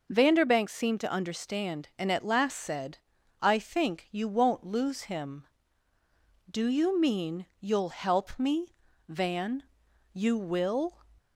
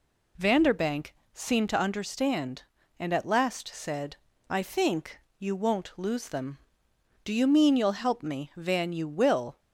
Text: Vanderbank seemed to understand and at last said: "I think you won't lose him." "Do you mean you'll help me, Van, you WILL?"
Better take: first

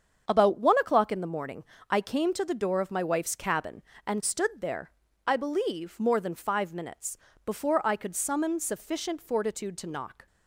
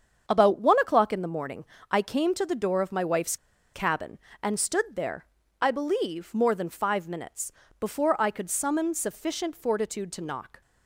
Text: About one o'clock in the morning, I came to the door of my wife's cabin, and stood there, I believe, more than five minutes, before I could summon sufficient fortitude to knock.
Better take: first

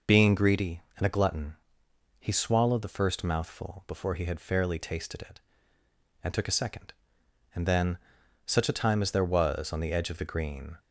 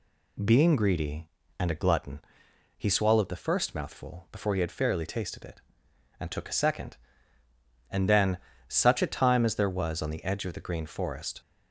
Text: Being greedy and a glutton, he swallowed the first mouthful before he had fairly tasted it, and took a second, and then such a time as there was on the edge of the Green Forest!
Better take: second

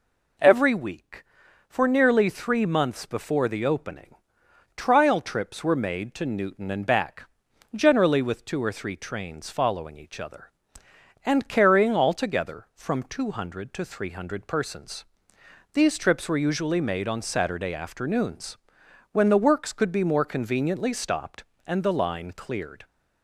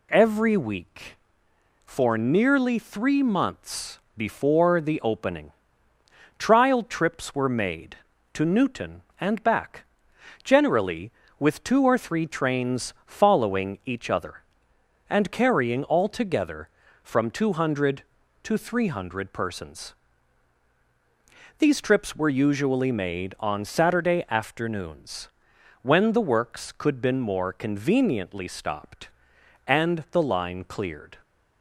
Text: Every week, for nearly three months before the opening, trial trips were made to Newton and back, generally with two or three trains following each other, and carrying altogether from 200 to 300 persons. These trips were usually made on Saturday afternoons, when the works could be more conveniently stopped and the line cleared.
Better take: first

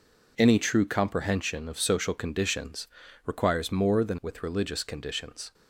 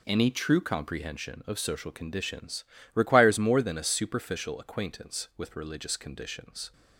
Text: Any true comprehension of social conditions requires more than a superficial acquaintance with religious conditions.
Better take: second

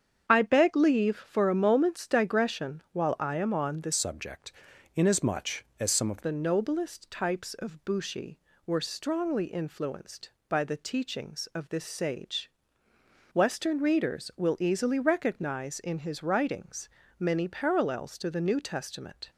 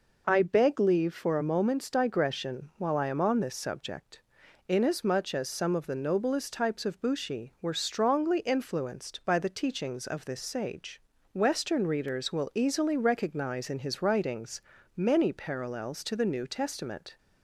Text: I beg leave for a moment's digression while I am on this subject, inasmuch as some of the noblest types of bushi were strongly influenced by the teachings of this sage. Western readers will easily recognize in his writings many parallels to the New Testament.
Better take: second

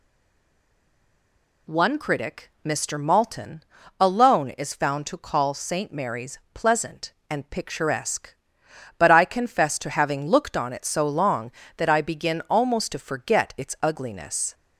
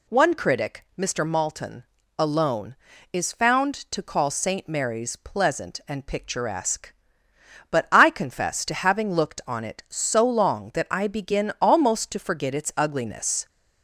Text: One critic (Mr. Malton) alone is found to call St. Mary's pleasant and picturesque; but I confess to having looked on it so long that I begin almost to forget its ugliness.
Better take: second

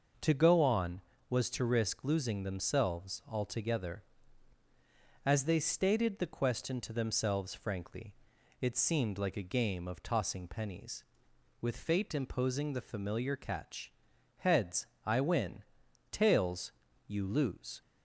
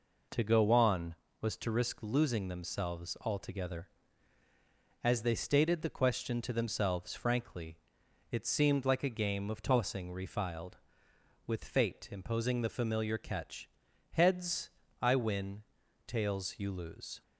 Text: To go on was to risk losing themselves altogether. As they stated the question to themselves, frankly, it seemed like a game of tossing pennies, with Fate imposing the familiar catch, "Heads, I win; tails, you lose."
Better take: first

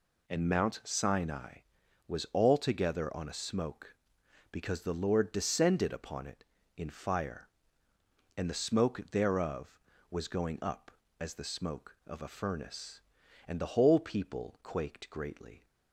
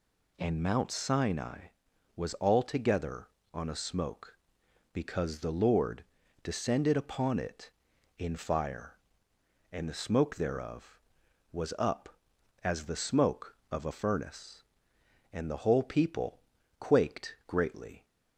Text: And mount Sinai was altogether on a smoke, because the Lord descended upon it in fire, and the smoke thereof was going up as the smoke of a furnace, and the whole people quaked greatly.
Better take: first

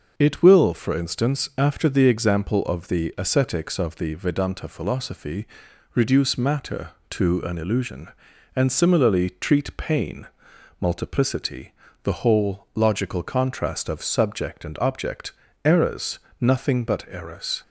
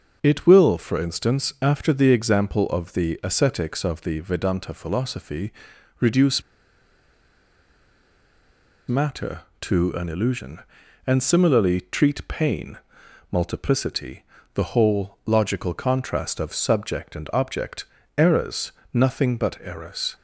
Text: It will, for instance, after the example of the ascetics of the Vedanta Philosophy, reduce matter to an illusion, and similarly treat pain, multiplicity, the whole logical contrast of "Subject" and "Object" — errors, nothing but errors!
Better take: first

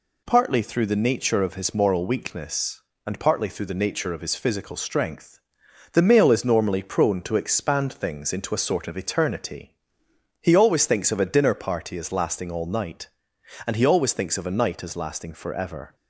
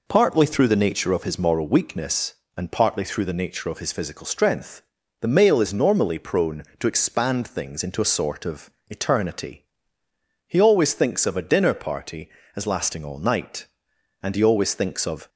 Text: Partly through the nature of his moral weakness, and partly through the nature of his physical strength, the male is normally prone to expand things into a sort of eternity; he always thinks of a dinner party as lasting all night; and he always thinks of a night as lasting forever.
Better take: first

